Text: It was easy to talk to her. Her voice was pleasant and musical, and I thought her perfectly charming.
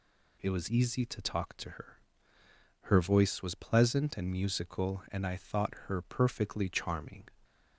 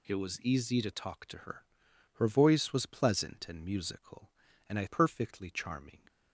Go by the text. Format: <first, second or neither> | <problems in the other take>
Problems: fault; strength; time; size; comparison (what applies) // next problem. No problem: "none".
first | skips "thought her"; at 4.8 s